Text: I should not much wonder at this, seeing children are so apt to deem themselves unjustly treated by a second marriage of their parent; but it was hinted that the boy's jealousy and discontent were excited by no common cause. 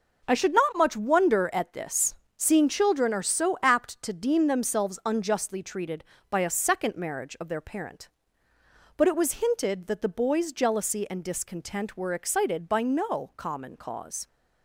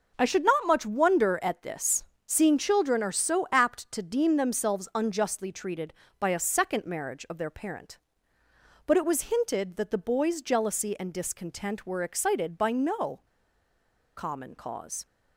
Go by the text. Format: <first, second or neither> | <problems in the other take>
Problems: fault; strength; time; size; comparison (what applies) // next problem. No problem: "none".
first | pauses between "no" and "common"; noticeable; at 13.2 s; 0.93 s long